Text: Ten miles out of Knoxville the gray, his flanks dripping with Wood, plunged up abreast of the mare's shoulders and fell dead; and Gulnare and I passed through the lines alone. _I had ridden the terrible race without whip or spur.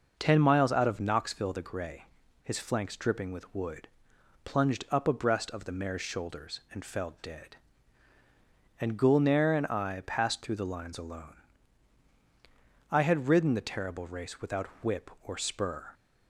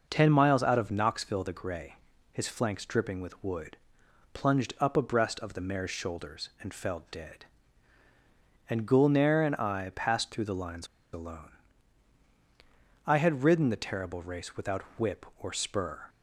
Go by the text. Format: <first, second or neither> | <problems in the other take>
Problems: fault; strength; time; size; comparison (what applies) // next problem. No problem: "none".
first | pauses between "lines" and "alone"; slight; at 10.8 s; 0.27 s long // pauses between "without" and "whip"; slight; at 14.8 s; 0.16 s long; slight in the first